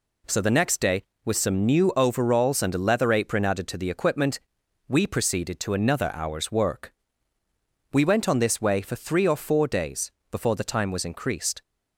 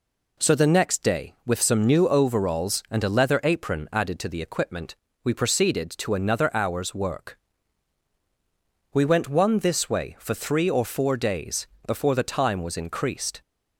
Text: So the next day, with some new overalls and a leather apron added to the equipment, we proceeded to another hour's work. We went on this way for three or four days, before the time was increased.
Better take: first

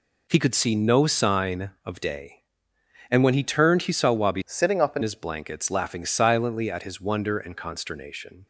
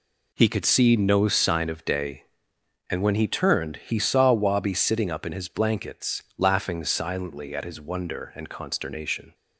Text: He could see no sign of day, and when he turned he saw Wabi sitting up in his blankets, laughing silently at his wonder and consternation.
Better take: second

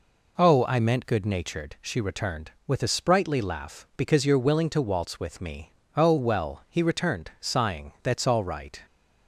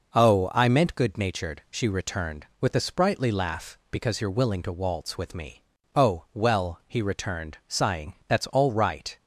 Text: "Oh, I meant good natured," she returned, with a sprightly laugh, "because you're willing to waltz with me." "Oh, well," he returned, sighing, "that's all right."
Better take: neither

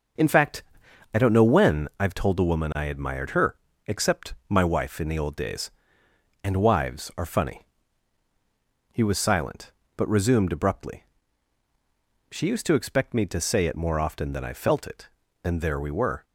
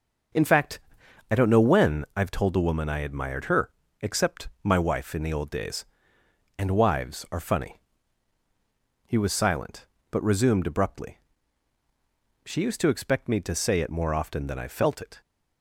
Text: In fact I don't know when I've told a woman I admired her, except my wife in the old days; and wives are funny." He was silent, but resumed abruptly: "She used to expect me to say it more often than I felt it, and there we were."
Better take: first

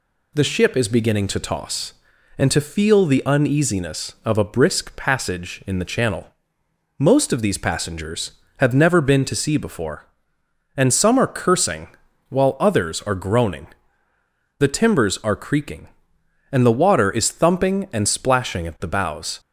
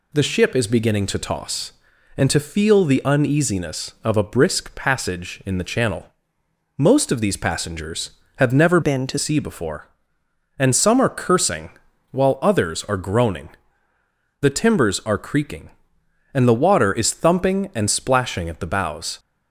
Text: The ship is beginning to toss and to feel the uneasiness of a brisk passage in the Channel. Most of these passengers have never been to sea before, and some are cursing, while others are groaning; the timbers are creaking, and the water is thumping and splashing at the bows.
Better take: first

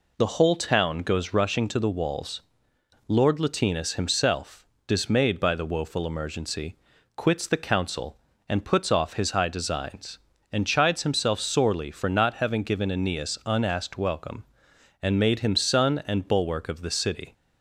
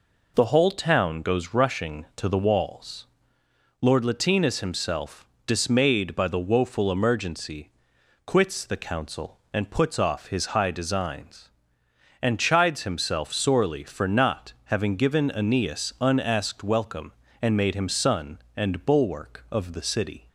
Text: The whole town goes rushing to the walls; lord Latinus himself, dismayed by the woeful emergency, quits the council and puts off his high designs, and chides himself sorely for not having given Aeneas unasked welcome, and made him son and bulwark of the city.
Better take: neither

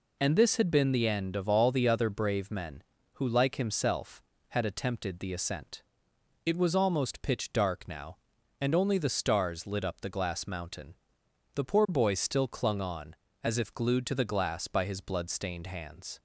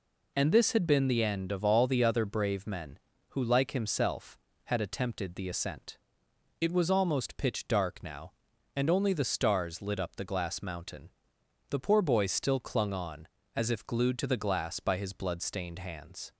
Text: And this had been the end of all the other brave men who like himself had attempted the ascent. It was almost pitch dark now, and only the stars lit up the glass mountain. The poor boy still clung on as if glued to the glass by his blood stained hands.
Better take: neither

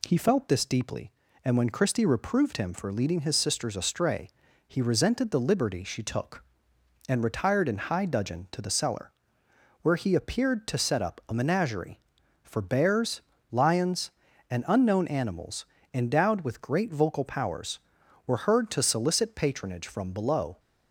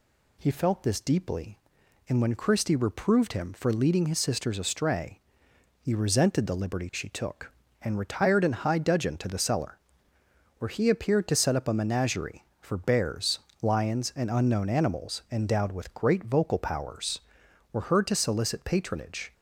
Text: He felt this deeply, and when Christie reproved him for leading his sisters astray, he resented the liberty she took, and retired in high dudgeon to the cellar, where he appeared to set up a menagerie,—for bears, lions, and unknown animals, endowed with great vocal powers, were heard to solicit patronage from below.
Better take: first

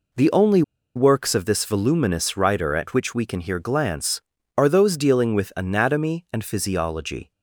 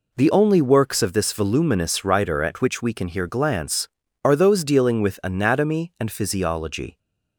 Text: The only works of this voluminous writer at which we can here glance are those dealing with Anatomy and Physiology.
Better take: second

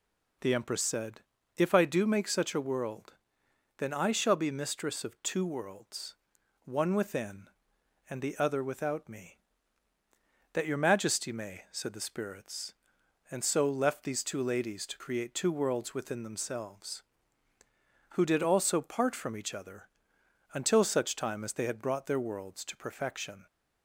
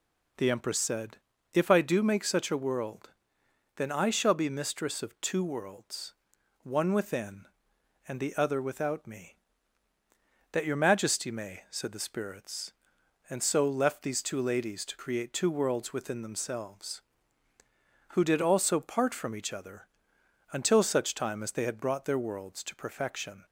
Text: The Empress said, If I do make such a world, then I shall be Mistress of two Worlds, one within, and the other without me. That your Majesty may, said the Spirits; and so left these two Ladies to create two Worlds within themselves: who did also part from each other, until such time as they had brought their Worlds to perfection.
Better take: neither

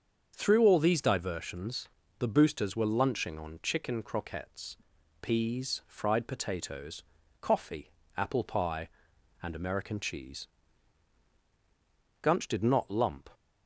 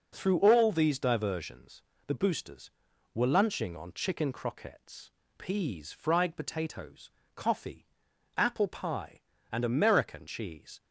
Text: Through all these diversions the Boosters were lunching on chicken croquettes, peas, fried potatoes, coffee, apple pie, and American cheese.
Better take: second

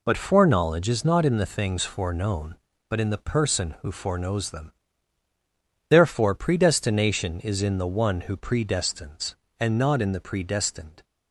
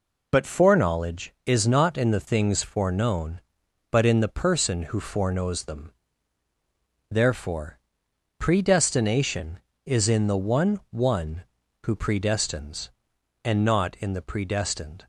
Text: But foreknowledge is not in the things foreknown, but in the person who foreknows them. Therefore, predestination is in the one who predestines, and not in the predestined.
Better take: first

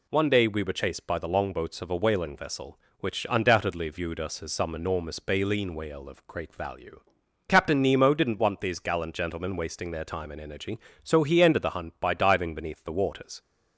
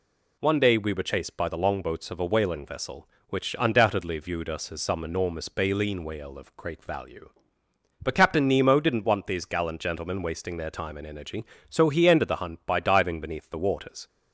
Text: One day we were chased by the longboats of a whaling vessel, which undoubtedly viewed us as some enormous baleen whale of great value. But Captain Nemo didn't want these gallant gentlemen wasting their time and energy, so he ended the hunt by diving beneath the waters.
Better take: second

